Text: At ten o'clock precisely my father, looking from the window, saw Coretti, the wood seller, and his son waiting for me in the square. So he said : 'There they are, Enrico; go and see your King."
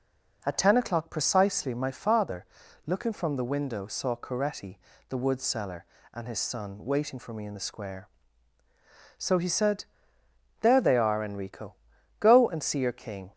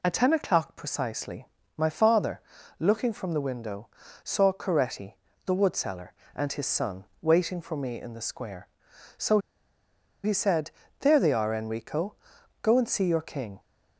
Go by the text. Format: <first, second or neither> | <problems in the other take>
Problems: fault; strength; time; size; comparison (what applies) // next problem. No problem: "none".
first | pauses between "precisely" and "my"; slight; at 1.4 s; 0.28 s long // pauses between "son" and "waiting"; slight; at 7.0 s; 0.18 s long // pauses between "So" and "he"; noticeable; at 9.3 s; 0.84 s long